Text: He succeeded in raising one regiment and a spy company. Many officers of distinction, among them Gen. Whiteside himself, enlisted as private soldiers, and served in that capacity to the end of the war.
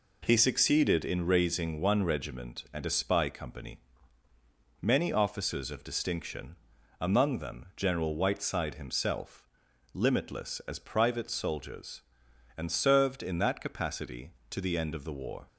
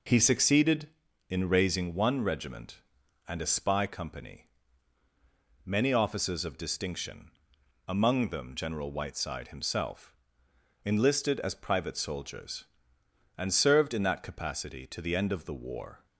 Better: second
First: says "limitless" for "enlisted"; at 9.9 s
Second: none

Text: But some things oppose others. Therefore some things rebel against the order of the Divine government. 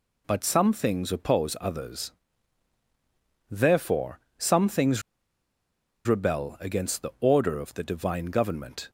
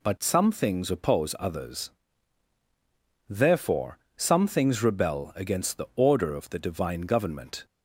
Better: second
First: pauses between "Therefore" and "some"; slight; at 4.1 s; 0.20 s long // pauses between "things" and "rebel"; at 5.0 s; 1.0 s long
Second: pauses between "Therefore" and "some"; slight; at 3.9 s; 0.20 s long

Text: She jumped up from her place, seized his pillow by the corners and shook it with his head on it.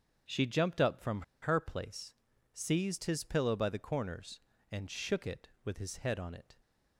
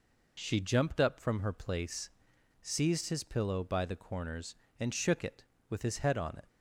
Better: second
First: starts louder than the rest; until 1.4 s; 7 dB // pauses between "from" and "her"; slight; at 1.2 s; 0.20 s long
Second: none

